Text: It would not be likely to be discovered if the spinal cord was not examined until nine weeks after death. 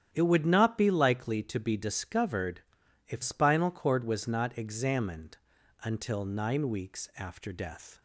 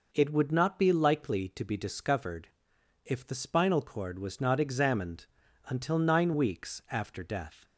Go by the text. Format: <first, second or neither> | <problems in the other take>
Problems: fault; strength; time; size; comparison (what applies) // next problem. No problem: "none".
second | starts louder than the rest; strong; until 1.1 s; 9.5 dB // pauses between "discovered" and "if"; noticeable; at 2.6 s; 0.46 s long; noticeable in the second // skips "the"; at 3.2 s // pauses between "examined" and "until"; noticeable; at 5.3 s; 0.46 s long; also in the second